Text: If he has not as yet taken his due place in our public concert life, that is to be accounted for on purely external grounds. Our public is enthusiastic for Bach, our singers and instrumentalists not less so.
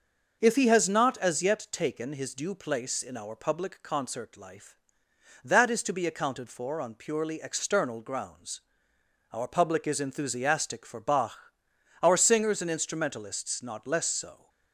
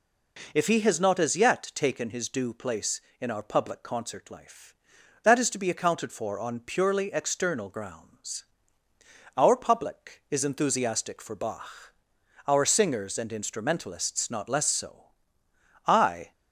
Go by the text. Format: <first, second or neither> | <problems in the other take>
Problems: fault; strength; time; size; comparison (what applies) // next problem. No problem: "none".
first | goes on to say "I"; slight; from 15.8 s on; 0.46 s long